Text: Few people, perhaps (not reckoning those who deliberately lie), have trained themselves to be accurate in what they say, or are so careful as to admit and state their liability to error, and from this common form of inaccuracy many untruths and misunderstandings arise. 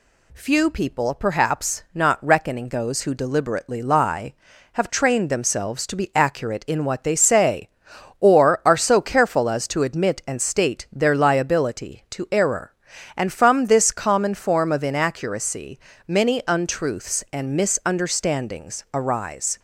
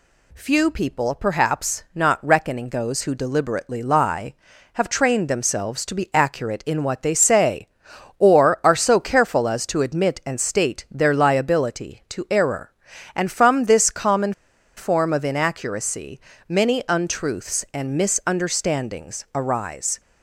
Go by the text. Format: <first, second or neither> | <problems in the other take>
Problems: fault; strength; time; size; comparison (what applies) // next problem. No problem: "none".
first | pauses between "common" and "form"; at 14.3 s; 0.45 s long // pauses between "inaccuracy" and "many"; slight; at 16.1 s; 0.28 s long; slight in the first